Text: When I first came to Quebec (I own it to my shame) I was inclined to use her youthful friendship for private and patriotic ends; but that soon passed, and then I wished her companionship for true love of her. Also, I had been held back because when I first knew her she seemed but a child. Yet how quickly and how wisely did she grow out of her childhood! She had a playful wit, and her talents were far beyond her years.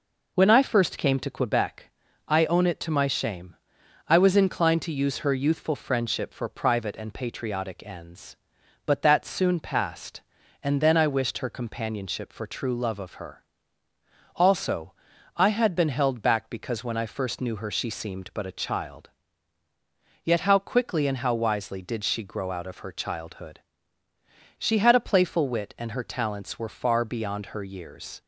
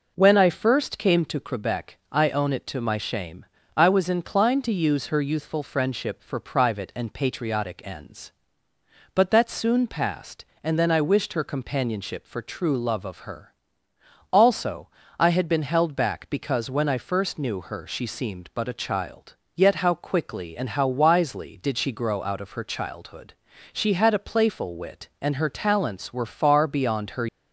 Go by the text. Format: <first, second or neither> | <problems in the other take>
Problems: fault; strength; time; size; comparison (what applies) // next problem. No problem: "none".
first | stops before "years"; at 27.2 s